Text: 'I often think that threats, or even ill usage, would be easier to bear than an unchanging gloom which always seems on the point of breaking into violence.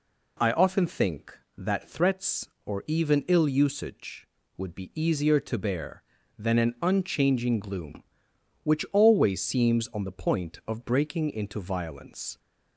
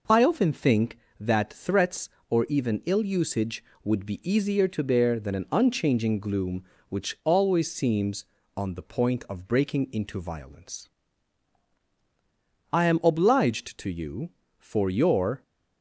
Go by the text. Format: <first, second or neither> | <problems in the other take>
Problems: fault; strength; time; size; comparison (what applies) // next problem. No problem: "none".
first | goes on to say "I am obliged to you for your"; strong; from 12.7 s on; 2.7 s long